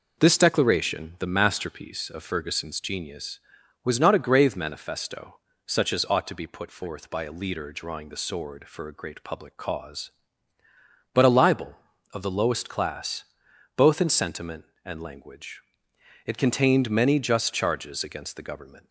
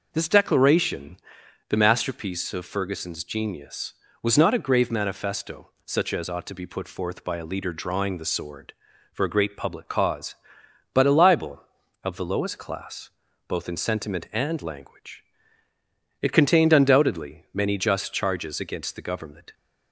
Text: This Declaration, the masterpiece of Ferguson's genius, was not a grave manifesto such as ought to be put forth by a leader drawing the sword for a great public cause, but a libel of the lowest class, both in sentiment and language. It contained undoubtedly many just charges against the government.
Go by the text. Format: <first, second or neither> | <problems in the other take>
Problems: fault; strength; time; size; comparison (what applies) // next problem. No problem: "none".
second | pauses between "manifesto" and "such"; slight; at 5.3 s; 0.28 s long; slight in the second // skips "undoubtedly"; at 16.8 s